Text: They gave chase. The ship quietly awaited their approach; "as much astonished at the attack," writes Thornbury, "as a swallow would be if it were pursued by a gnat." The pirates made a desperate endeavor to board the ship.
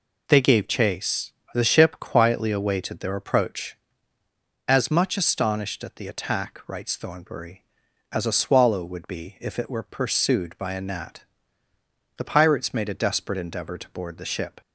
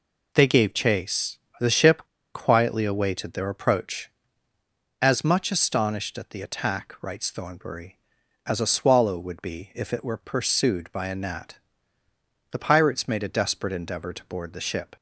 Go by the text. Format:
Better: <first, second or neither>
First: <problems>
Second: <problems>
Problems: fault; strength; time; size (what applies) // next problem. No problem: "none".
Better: first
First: none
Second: pauses between "ship" and "quietly"; slight; at 2.0 s; 0.27 s long